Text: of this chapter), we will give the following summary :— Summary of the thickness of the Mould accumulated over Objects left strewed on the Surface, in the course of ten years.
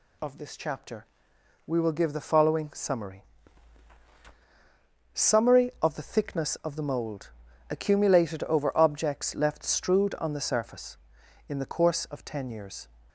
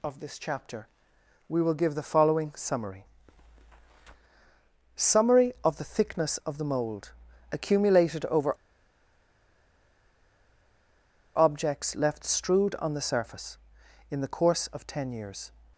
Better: first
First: pauses between "Mould" and "accumulated"; at 7.3 s; 0.40 s long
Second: pauses between "Mould" and "accumulated"; at 7.1 s; 0.40 s long // pauses between "over" and "Objects"; strong; at 8.5 s; 2.8 s long

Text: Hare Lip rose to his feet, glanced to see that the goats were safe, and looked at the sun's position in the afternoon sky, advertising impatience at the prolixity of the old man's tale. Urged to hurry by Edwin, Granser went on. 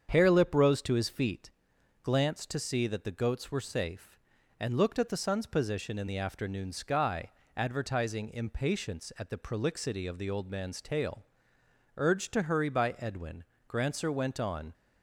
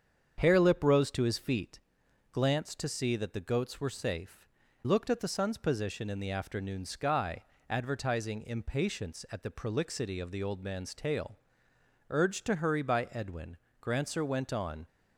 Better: first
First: starts louder than the rest; strong; until 1.1 s; 7.5 dB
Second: starts louder than the rest; strong; until 1.3 s; 7.5 dB // skips "and"; at 4.6 s

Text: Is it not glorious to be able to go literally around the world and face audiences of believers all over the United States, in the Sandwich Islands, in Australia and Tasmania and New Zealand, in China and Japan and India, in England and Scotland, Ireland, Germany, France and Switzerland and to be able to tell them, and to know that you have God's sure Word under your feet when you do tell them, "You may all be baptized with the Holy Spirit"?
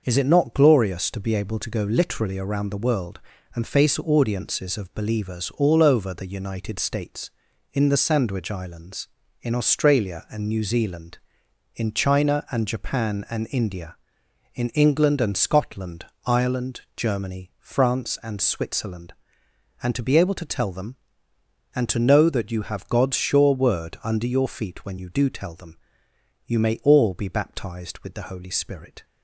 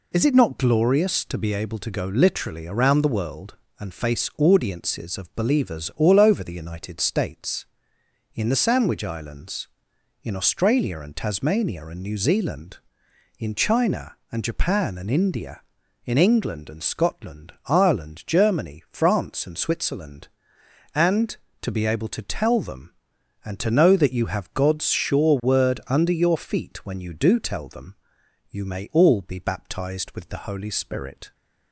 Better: second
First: starts louder than the rest; noticeable; until 1.0 s; 6 dB // skips "Tasmania and"; at 10.4 s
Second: none

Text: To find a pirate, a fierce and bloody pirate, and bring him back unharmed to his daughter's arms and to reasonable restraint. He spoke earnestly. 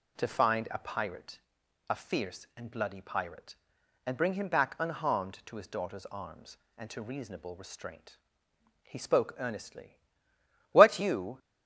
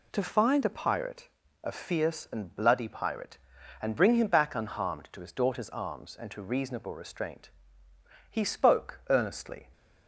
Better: second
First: goes on to say "What you"; noticeable; from 10.7 s on; 0.66 s long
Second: none

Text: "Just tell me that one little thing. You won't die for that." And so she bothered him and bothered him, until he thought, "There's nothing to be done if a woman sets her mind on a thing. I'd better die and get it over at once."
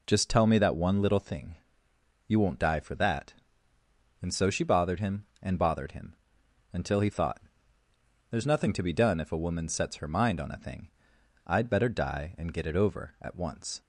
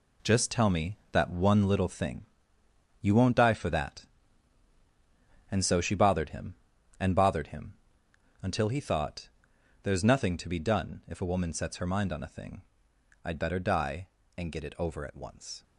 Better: first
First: none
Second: gets quieter; strong; throughout; 9 dB

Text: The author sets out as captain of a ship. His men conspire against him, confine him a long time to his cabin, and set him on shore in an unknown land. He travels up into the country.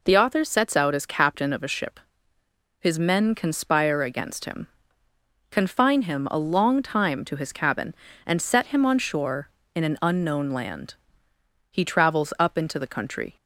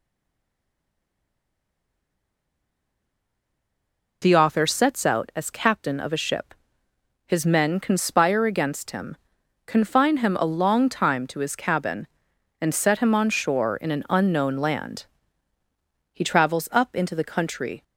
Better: first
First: none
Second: stays silent before the first word; strong; until 4.2 s; 4.2 s long

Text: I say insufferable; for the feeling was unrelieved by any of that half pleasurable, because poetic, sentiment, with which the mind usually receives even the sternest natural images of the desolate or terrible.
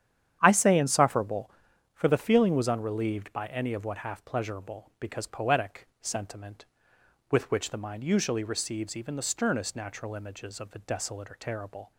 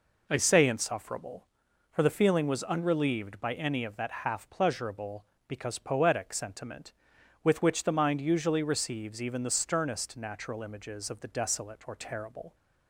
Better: second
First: starts louder than the rest; strong; until 1.4 s; 9.5 dB // says "what" for "that"; at 3.8 s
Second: none

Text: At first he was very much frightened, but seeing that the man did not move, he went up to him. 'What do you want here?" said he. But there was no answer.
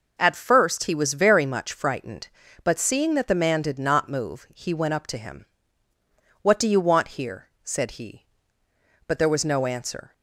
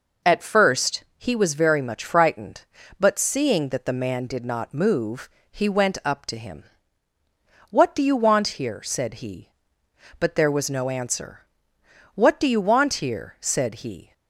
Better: first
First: none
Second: goes on to say "What do you want here said he"; strong; from 12.1 s on; 1.9 s long

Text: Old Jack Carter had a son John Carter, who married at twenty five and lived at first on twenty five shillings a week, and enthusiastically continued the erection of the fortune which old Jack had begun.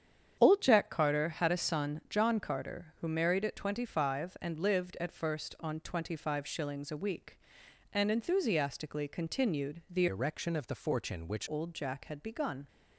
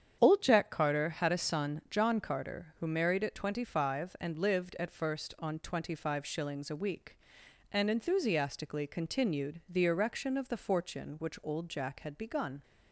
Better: second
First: starts louder than the rest; strong; until 1.4 s; 8 dB // changes voice from "erection" to "which"; from 10.0 to 11.4 s; 1.4 s long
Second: starts louder than the rest; strong; until 1.2 s; 8 dB

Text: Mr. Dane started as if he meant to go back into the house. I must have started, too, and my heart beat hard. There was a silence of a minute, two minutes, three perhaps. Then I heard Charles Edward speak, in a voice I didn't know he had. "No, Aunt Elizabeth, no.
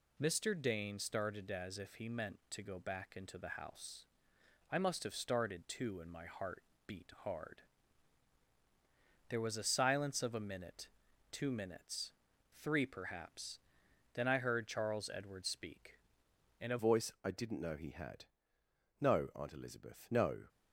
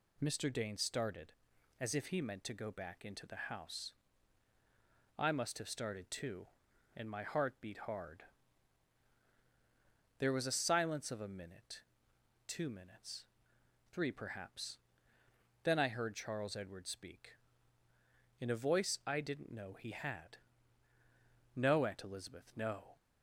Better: second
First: pauses between "heart" and "beat"; slight; at 6.6 s; 0.24 s long // changes voice at "voice"; from 16.7 s on; 3.7 s long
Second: none

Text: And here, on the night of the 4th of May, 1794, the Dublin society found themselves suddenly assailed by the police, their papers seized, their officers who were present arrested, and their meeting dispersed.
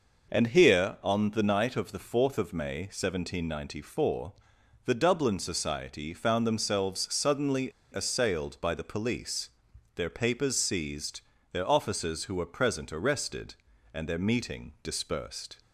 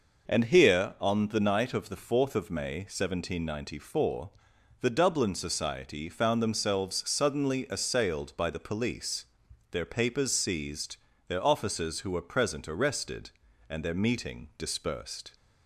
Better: second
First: pauses between "suddenly" and "assailed"; slight; at 7.7 s; 0.21 s long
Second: none

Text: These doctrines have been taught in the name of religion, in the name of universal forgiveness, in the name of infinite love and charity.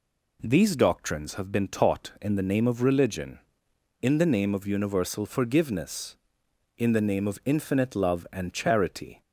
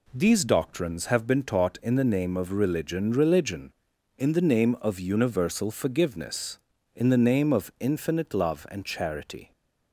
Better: first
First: none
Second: says "religion" twice; at 3.1 s

